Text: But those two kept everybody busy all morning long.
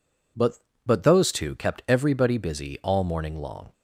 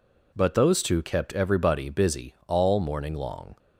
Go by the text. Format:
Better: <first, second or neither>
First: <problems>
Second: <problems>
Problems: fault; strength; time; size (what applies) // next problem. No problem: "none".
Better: second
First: says "But" twice; at 0.8 s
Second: none